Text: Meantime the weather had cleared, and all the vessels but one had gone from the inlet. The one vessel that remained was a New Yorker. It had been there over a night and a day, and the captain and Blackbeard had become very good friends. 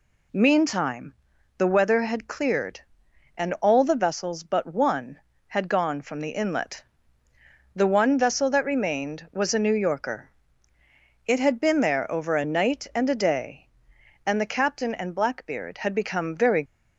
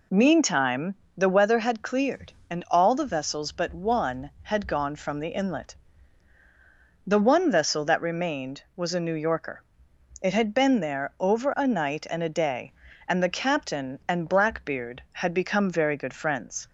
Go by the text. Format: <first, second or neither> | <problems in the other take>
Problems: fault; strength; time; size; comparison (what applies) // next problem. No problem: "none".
second | pauses between "Meantime" and "the"; noticeable; at 1.1 s; 0.46 s long; slight in the second // stops before "good friends"; at 16.6 s